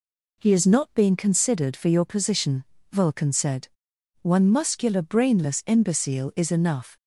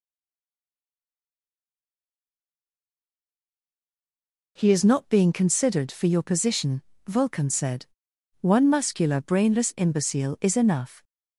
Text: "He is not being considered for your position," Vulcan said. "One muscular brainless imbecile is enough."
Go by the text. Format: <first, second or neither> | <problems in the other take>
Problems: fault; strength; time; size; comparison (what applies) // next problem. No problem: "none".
first | stays silent before the first word; strong; until 4.5 s; 4.5 s long